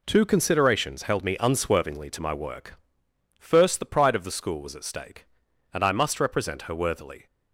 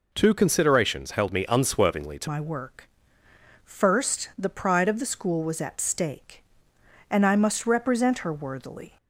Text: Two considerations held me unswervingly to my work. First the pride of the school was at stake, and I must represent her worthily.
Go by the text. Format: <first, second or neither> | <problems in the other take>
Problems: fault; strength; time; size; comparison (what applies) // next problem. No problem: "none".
first | changes voice at "my"; from 2.2 s on; 6.7 s long